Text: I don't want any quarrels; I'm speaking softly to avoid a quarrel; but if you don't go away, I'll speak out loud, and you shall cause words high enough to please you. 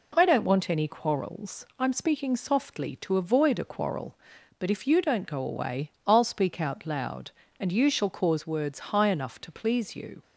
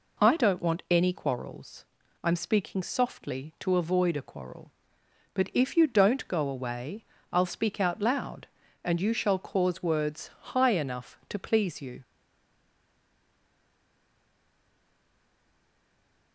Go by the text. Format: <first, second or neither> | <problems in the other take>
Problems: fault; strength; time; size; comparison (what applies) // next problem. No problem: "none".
first | stays silent after the last word; strong; from 12.0 s on; 4.3 s long